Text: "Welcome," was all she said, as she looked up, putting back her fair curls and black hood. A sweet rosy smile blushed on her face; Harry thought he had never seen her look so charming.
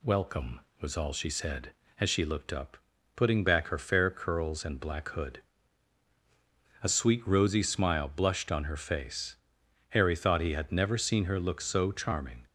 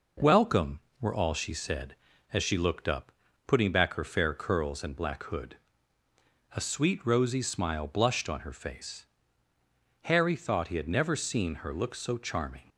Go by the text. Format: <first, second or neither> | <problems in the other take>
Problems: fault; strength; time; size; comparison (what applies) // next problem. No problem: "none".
first | says "were" for "was"; at 1.0 s